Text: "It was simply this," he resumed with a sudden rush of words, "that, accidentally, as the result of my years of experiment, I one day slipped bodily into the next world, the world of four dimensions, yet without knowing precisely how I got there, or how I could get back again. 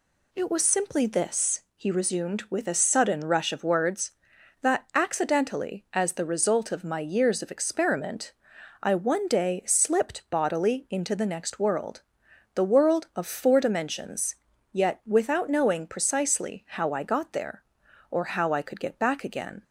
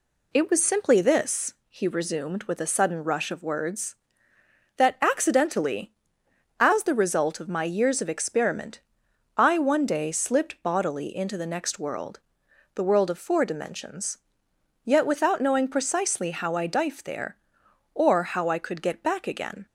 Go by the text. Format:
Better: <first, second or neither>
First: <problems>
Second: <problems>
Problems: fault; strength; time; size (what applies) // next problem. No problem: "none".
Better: first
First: none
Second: says "dife" for "got"; at 16.6 s